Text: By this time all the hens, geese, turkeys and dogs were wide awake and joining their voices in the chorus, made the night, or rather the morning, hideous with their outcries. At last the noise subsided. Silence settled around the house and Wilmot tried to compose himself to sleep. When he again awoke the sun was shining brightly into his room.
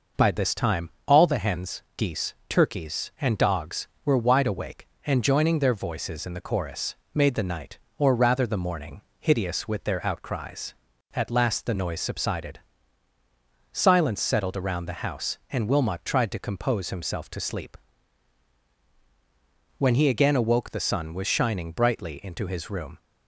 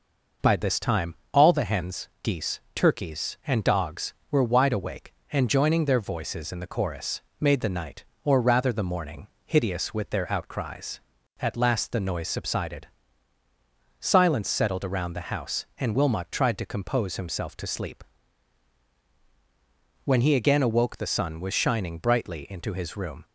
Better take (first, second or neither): neither